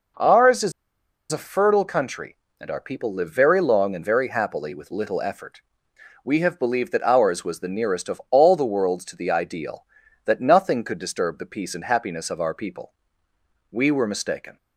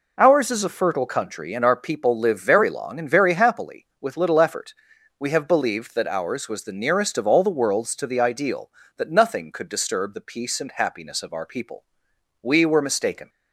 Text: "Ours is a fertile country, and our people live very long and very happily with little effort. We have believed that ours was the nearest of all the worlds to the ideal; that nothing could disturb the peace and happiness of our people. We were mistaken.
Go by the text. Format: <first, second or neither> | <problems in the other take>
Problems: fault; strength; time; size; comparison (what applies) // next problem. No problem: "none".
second | pauses between "is" and "a"; noticeable; at 0.7 s; 0.60 s long